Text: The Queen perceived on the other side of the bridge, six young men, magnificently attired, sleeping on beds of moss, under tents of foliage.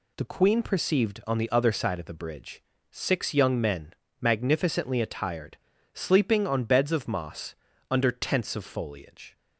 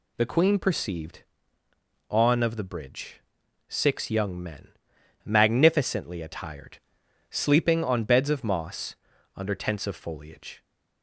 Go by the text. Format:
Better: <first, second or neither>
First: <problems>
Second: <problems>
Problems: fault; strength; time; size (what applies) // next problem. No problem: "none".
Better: first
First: none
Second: skips "the other side"; at 2.4 s